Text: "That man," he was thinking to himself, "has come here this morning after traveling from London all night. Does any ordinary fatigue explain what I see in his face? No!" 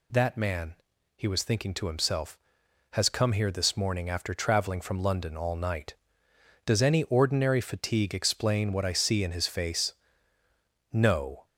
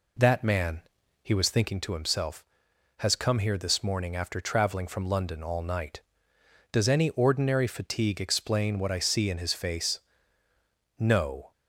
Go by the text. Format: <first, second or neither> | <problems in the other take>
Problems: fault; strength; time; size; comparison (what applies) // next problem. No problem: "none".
first | starts louder than the rest; until 1.8 s; 3.5 dB